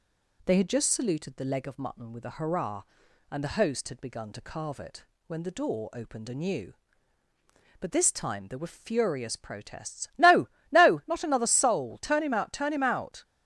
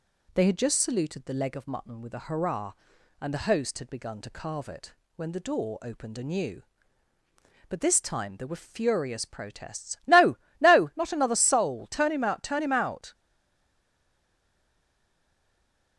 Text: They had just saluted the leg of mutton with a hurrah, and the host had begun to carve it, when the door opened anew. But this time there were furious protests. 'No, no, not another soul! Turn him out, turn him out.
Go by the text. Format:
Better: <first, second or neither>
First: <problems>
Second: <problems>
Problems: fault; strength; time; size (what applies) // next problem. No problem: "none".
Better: first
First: none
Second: stays silent after the last word; strong; from 13.1 s on; 2.8 s long